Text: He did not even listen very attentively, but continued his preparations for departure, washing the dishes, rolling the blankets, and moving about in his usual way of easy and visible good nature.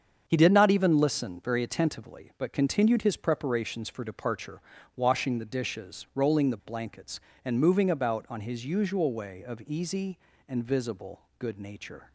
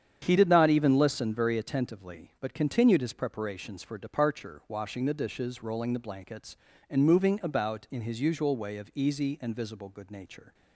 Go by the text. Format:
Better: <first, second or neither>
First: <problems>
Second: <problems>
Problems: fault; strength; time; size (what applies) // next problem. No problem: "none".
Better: second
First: starts louder than the rest; strong; until 1.2 s; 7 dB // says "on" for "in"; at 8.2 s // pauses between "visible" and "good"; slight; at 11.1 s; 0.18 s long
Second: starts louder than the rest; strong; until 1.2 s; 8.5 dB